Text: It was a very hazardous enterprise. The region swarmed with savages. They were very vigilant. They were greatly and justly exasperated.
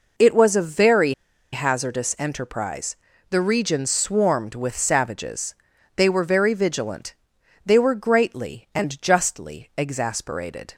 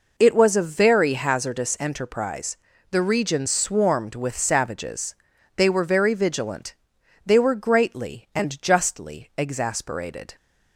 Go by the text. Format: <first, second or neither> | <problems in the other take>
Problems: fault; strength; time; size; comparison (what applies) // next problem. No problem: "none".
second | pauses between "very" and "hazardous"; at 1.1 s; 0.40 s long